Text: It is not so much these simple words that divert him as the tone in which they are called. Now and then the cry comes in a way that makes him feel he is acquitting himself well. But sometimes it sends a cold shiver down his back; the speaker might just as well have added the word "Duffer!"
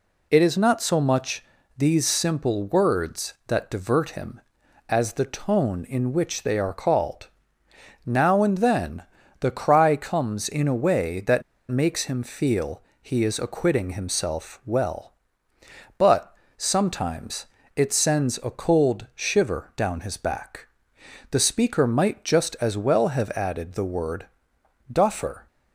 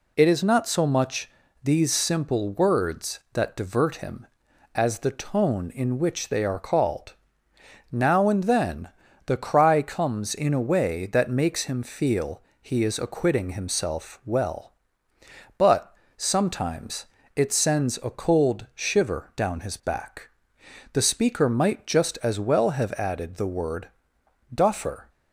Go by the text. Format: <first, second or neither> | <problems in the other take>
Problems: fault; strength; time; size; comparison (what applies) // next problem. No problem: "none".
second | pauses between "much" and "these"; slight; at 1.4 s; 0.32 s long; slight in the second // pauses between "then" and "the"; at 9.0 s; 0.38 s long; also in the second // pauses between "that" and "makes"; slight; at 11.4 s; 0.28 s long // pauses between "feel" and "he"; slight; at 12.8 s; 0.18 s long; slight in the second // pauses between "But" and "sometimes"; slight; at 16.3 s; 0.22 s long; slight in the second // pauses between "sometimes" and "it"; slight; at 17.4 s; 0.28 s long; slight in the second // pauses between "word" and "Duffer"; noticeable; at 24.2 s; 0.66 s long; noticeable in the second